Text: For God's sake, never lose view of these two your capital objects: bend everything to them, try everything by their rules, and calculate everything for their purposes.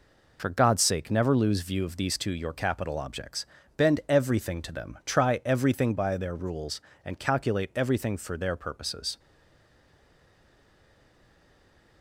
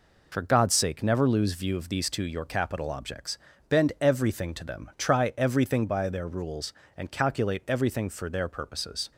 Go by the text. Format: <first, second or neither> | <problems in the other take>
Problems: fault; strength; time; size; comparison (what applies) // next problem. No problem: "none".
second | stays silent after the last word; strong; from 9.1 s on; 2.9 s long